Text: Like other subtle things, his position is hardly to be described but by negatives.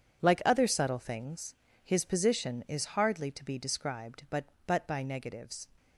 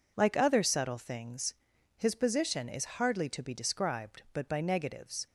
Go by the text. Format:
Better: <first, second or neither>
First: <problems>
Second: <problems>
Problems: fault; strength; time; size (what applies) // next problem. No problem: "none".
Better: second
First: says "but" twice; at 4.6 s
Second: none